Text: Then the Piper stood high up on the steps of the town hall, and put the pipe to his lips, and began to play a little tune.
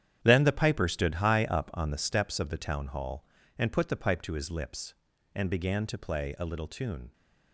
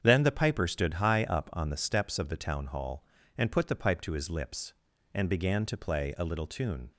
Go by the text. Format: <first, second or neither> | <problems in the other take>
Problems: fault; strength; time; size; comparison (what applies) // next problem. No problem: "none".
second | gets quieter; strong; throughout; 11.5 dB // starts louder than the rest; strong; until 1.2 s; 9.5 dB; strong in the second